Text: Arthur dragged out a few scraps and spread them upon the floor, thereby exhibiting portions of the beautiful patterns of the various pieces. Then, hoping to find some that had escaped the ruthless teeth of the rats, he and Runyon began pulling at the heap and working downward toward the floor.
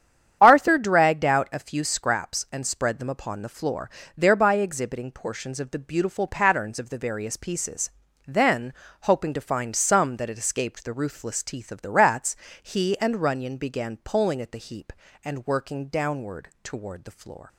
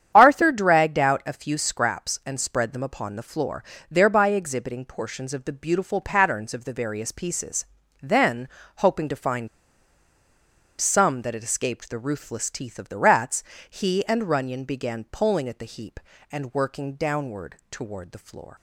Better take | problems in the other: first | starts louder than the rest; strong; until 1.1 s; 9 dB; strong in the first // pauses between "find" and "some"; strong; at 9.4 s; 1.3 s long // pauses between "downward" and "toward"; slight; at 17.5 s; 0.16 s long; slight in the first

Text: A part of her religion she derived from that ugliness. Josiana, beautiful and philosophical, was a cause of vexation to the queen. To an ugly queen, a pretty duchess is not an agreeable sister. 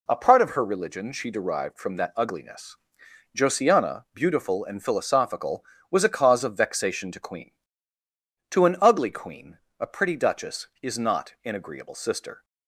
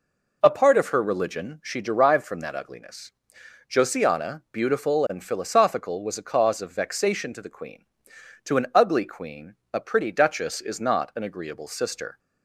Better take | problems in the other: second | skips "the"; at 7.1 s

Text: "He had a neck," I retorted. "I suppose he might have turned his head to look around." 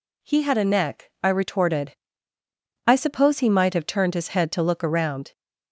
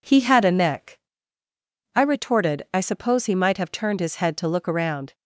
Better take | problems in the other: neither | none

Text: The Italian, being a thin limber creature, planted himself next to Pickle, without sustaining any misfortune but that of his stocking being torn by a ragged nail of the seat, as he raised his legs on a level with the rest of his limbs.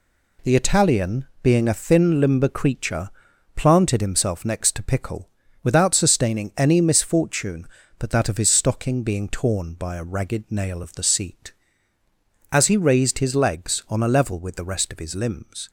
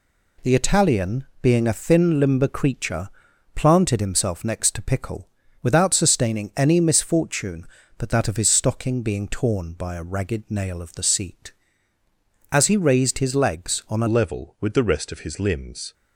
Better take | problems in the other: first | changes voice at "level"; from 14.0 s on; 1.9 s long

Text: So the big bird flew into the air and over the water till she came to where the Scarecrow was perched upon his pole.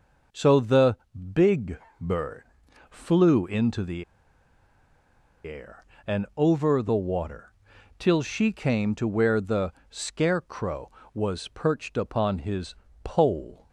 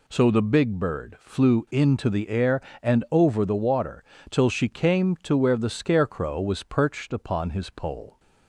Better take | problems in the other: second | pauses between "the" and "big"; at 0.9 s; 0.38 s long // pauses between "big" and "bird"; slight; at 1.7 s; 0.22 s long // pauses between "bird" and "flew"; noticeable; at 2.4 s; 0.46 s long // pauses between "the" and "air"; strong; at 4.0 s; 1.4 s long // pauses between "water" and "till"; noticeable; at 7.5 s; 0.46 s long; slight in the second // pauses between "the" and "Scarecrow"; slight; at 9.7 s; 0.16 s long // pauses between "his" and "pole"; slight; at 12.7 s; 0.28 s long

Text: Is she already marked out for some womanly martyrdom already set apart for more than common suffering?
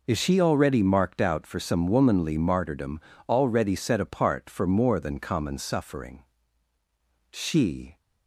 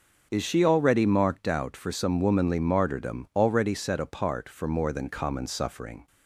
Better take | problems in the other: second | pauses between "martyrdom" and "already"; slight; at 2.9 s; 0.30 s long // goes on to say "She"; noticeable; from 7.3 s on; 0.66 s long

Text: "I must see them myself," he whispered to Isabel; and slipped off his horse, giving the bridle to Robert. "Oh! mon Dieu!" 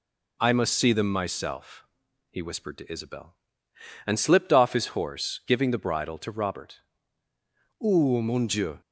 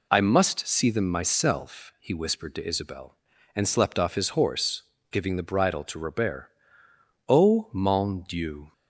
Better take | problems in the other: first | says "slept" for "slipped"; at 3.6 s

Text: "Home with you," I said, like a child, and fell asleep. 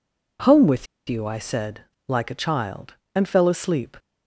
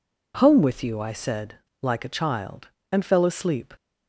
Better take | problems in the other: second | pauses between "with" and "you"; slight; at 0.8 s; 0.23 s long

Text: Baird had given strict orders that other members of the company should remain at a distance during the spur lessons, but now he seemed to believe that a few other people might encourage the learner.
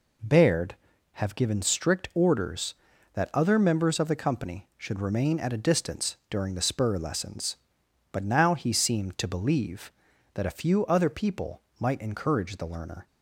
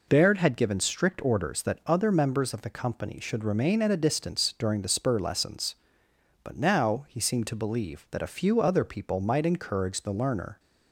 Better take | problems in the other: second | says "have" for "had"; at 1.1 s // pauses between "people" and "might"; slight; at 11.6 s; 0.18 s long

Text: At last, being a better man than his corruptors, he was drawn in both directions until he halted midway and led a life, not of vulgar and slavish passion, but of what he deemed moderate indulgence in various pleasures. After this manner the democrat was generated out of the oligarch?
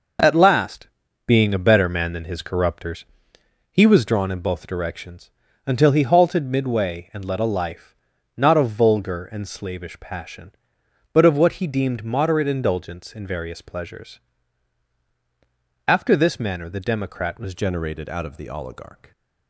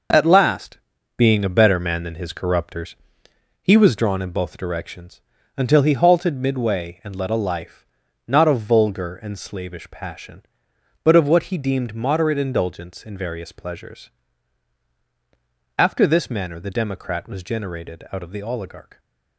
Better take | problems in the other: second | pauses between "directions" and "until"; slight; at 5.3 s; 0.34 s long; slight in the second // changes voice at "generated"; from 17.5 s on; 1.6 s long

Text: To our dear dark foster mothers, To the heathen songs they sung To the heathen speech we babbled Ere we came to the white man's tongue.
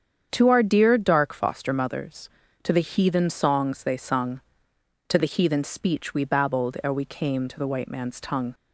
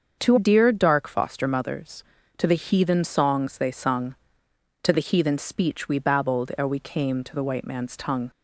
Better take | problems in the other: first | starts louder than the rest; until 1.2 s; 6.5 dB; strong in the first // skips "our"; at 0.3 s

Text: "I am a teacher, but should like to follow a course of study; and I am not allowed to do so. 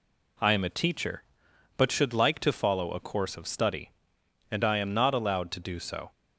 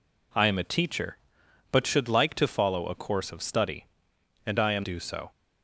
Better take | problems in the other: first | skips "not allowed to"; at 4.8 s

